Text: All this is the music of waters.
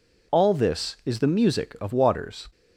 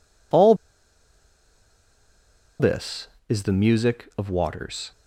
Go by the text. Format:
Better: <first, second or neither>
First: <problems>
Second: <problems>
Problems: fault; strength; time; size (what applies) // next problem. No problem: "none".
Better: first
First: none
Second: pauses between "All" and "this"; strong; at 0.5 s; 2.0 s long